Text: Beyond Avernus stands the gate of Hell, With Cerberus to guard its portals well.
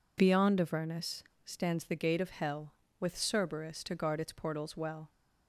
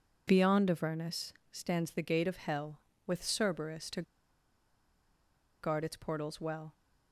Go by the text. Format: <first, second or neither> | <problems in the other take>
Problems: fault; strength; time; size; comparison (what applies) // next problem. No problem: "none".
first | pauses between "Avernus" and "stands"; slight; at 1.3 s; 0.18 s long; slight in the first // pauses between "to" and "guard"; strong; at 4.0 s; 1.5 s long